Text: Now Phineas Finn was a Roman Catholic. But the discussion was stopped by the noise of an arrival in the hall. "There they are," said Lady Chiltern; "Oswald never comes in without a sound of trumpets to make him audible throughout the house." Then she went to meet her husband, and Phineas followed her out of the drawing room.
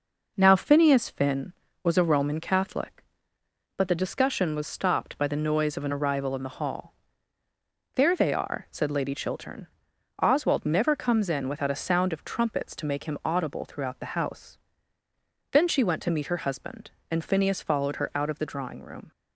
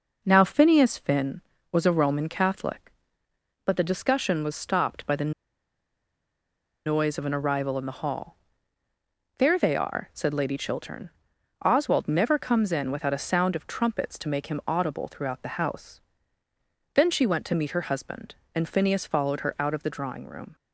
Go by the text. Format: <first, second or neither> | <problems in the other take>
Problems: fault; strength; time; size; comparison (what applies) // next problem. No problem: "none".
first | pauses between "the" and "noise"; strong; at 5.3 s; 1.5 s long